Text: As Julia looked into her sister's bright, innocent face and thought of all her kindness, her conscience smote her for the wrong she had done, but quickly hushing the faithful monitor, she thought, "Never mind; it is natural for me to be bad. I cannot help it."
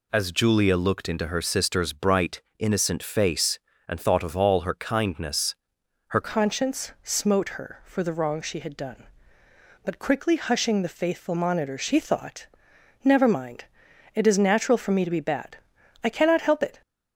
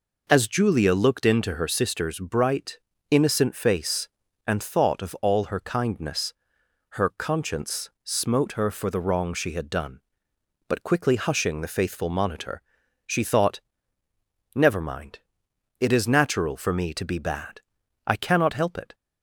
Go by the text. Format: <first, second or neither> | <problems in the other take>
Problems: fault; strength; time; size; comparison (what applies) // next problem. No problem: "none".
second | changes voice at "conscience"; from 6.2 s on; 10.6 s long